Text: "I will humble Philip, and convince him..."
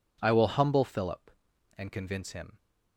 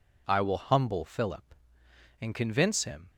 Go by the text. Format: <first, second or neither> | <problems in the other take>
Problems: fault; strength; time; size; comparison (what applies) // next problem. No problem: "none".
neither | none